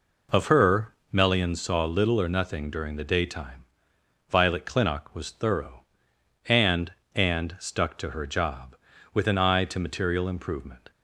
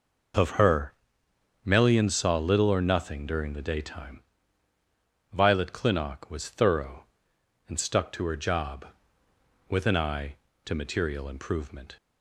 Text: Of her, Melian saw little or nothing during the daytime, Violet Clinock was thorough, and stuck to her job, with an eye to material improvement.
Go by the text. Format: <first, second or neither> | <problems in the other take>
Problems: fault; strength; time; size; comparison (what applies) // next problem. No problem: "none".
second | says "and" twice; at 7.1 s